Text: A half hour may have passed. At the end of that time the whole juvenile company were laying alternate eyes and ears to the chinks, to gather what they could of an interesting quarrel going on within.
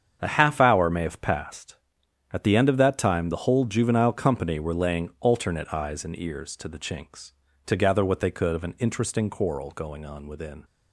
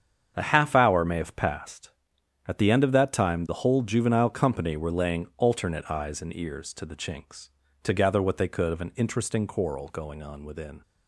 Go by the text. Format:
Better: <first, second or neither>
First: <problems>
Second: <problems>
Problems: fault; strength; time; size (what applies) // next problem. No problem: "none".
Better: neither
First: starts louder than the rest; strong; until 1.2 s; 7.5 dB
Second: starts louder than the rest; strong; until 1.3 s; 7.5 dB